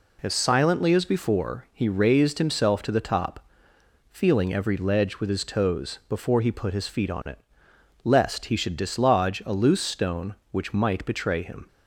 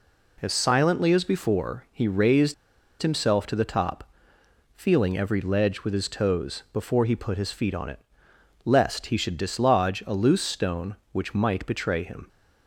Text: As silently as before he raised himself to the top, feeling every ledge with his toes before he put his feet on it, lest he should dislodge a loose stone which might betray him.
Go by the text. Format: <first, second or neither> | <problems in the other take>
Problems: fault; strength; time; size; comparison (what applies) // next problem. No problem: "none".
first | pauses between "raised" and "himself"; noticeable; at 2.5 s; 0.47 s long